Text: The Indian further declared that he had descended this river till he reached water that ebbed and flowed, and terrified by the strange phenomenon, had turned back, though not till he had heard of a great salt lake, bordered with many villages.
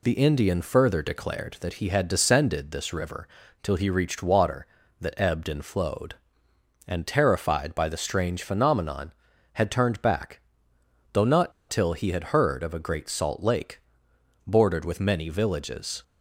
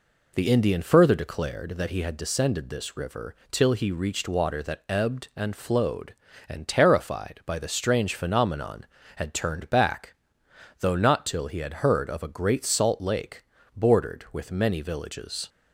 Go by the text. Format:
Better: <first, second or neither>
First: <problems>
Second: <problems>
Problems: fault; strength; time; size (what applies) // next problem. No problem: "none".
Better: second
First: pauses between "river" and "till"; slight; at 3.2 s; 0.36 s long // pauses between "not" and "till"; slight; at 11.5 s; 0.18 s long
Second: pauses between "river" and "till"; slight; at 3.3 s; 0.16 s long